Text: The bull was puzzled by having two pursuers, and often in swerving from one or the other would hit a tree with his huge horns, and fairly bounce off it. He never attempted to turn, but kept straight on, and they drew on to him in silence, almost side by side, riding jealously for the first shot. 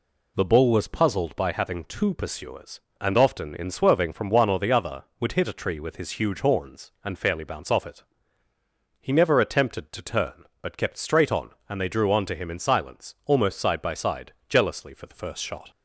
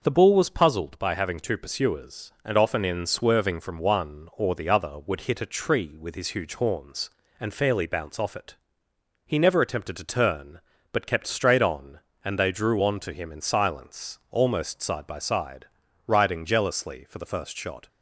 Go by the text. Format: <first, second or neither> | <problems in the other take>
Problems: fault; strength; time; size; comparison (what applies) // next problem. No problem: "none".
second | skips "riding"; at 14.4 s